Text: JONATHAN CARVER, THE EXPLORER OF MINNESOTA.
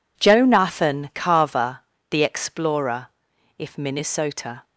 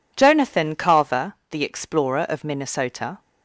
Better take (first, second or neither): second